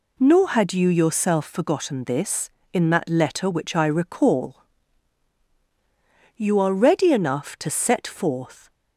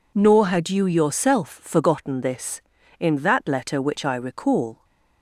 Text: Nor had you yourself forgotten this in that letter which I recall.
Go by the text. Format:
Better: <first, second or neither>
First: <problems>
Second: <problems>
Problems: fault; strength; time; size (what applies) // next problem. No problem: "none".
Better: second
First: goes on to say "You are ready enough to set forth"; strong; from 6.3 s on; 2.3 s long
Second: none